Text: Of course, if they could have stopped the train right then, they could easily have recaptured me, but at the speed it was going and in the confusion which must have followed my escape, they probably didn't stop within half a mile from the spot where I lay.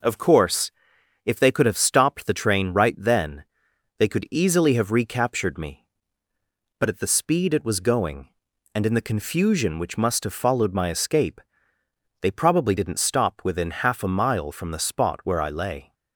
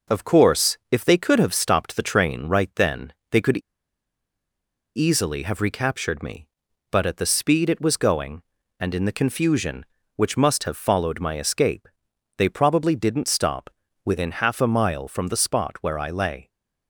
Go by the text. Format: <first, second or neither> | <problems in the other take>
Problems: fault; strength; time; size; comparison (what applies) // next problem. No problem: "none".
first | pauses between "could" and "easily"; strong; at 3.5 s; 1.3 s long // pauses between "stop" and "within"; slight; at 13.6 s; 0.36 s long